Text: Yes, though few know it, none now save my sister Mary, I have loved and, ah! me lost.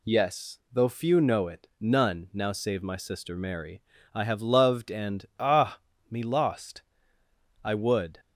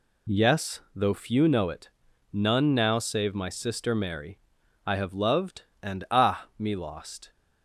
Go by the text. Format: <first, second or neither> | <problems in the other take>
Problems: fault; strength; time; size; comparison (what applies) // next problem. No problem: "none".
second | goes on to say "I would"; from 7.6 s on; 0.56 s long